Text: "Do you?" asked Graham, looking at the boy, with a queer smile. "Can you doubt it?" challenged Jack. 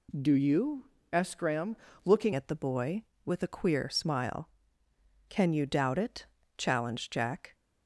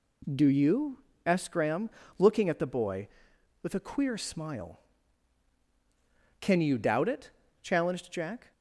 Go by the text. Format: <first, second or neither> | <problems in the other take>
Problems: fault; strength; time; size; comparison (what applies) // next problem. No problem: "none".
second | changes voice at "at"; from 2.3 s on; 5.2 s long